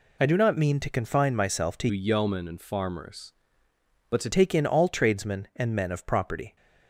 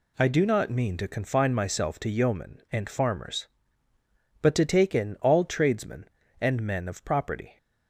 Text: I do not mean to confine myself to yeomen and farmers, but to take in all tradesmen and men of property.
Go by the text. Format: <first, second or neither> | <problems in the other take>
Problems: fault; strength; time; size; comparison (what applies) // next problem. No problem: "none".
second | changes voice from "yeomen" to "to"; from 1.9 to 4.2 s; 2.3 s long